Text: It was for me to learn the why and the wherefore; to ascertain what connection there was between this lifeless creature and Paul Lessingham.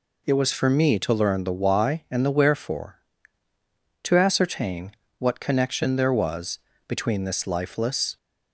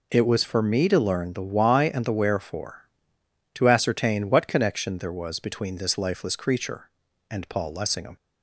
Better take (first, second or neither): second